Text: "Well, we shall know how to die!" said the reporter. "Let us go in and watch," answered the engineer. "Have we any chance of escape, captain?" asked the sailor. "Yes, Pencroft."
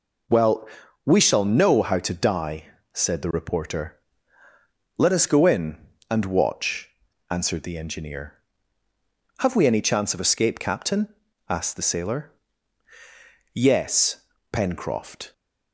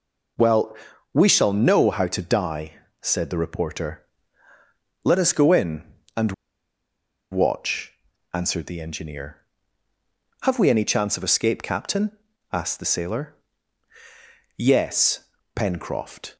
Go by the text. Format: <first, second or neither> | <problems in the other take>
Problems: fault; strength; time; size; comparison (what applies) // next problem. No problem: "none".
first | pauses between "and" and "watch"; at 6.3 s; 0.98 s long